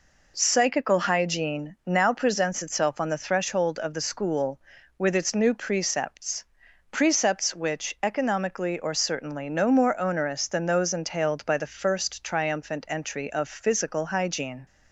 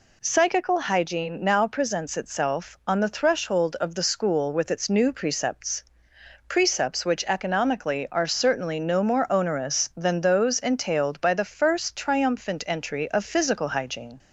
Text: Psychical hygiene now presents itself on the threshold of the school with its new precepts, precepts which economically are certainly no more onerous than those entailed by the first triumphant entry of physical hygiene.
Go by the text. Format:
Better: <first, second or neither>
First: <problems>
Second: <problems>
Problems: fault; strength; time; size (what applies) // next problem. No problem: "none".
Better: second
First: says "or" for "are"; at 8.7 s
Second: none